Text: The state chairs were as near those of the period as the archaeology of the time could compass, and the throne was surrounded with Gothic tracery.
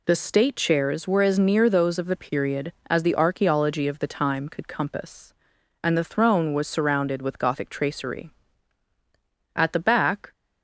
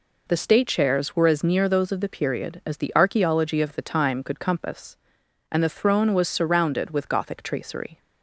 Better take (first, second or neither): second